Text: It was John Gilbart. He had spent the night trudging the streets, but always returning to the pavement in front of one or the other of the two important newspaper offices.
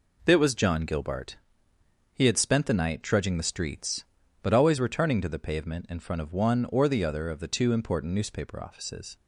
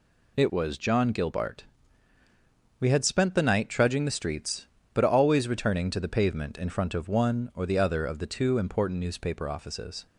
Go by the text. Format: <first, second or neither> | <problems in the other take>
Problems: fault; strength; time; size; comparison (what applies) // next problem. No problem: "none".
first | says "We" for "He"; at 2.7 s